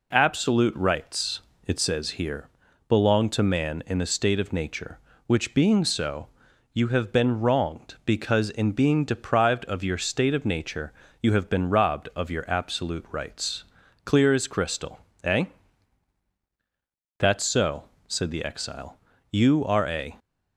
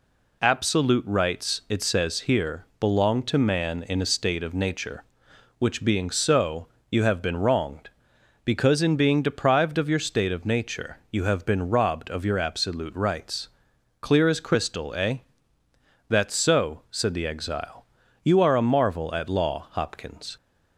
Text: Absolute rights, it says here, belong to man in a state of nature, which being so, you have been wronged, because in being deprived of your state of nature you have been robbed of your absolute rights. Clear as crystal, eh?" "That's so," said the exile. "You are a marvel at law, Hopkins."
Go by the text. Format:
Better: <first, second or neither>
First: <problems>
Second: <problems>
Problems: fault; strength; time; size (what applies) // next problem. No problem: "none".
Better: second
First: pauses between "nature" and "you"; slight; at 10.9 s; 0.30 s long // stops before "marvel at law Hopkins"; at 20.1 s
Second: none